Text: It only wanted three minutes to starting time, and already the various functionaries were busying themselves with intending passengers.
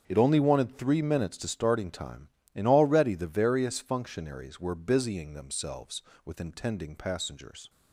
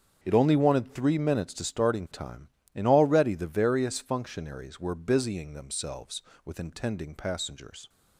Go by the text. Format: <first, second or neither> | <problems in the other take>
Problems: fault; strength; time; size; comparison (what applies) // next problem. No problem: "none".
neither | starts louder than the rest; strong; the same in both